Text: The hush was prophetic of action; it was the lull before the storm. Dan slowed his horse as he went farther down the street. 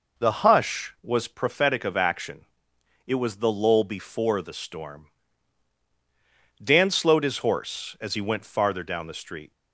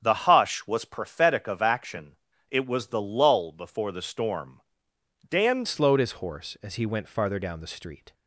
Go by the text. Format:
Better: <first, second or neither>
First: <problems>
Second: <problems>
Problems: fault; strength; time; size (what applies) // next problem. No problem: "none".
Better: first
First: none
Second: starts louder than the rest; strong; until 1.0 s; 8 dB // changes voice at "slowed"; from 5.6 s on; 2.5 s long